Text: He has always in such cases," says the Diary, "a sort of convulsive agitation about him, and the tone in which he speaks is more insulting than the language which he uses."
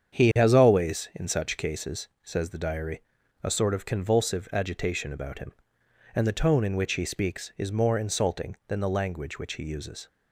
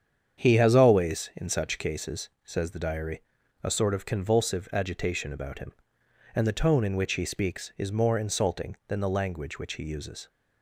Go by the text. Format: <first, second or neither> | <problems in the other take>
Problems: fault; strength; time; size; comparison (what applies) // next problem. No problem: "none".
neither | starts louder than the rest; strong; the same in both